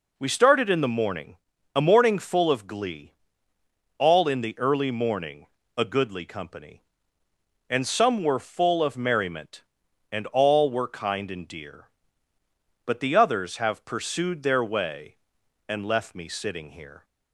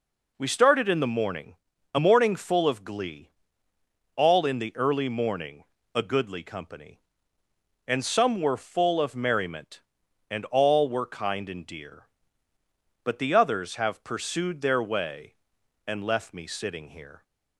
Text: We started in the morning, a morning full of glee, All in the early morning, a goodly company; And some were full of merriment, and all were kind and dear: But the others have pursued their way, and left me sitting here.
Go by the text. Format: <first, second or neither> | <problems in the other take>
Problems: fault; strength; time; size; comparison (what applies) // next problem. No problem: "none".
neither | none